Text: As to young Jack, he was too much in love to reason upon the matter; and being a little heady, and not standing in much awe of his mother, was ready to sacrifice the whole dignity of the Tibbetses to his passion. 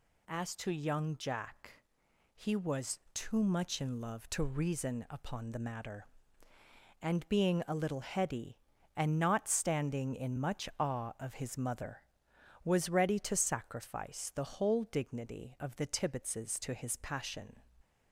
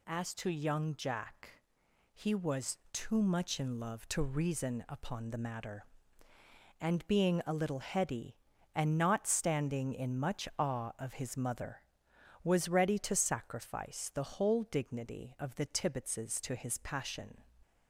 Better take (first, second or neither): neither